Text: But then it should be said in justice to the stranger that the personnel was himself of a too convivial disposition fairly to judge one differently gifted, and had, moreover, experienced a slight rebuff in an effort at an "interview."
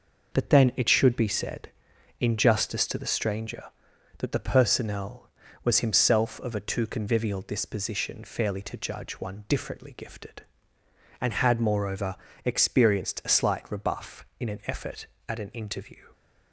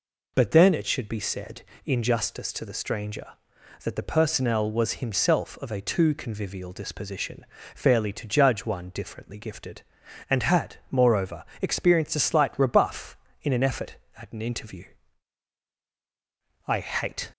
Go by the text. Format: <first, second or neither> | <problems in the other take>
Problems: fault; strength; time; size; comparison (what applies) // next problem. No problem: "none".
first | pauses between "disposition" and "fairly"; slight; at 7.4 s; 0.28 s long // goes on to say "I hate"; noticeable; from 16.6 s on; 0.64 s long